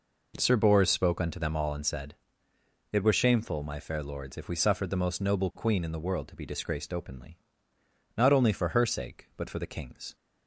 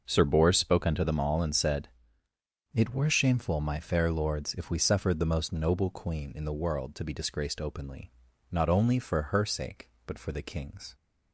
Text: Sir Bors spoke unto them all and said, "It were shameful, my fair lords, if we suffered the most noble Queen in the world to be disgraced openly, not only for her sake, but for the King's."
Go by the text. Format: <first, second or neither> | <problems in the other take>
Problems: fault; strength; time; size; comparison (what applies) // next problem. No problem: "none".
neither | none